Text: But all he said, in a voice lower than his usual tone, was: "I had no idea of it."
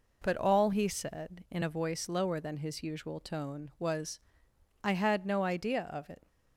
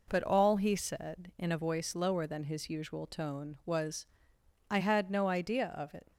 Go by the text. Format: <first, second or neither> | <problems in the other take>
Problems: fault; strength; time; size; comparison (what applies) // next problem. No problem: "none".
neither | none